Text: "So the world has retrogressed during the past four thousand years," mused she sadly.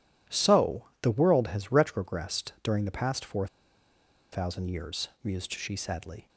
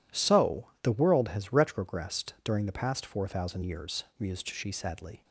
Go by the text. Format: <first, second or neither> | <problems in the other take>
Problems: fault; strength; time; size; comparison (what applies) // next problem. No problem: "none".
second | pauses between "So" and "the"; slight; at 0.8 s; 0.16 s long // pauses between "four" and "thousand"; noticeable; at 3.4 s; 0.85 s long